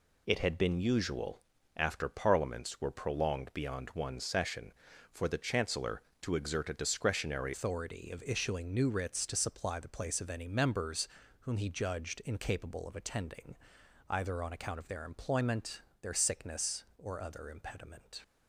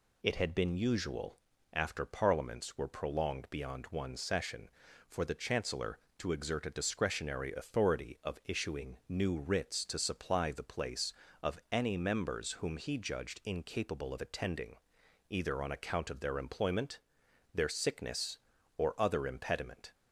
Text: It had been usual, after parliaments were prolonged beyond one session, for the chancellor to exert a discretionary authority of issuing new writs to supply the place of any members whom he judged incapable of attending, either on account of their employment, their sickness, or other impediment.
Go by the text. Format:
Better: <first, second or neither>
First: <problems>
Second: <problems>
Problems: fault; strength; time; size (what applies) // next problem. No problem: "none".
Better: second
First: changes voice at "authority"; from 7.5 s on; 10.7 s long // pauses between "members" and "whom"; slight; at 11.0 s; 0.32 s long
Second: none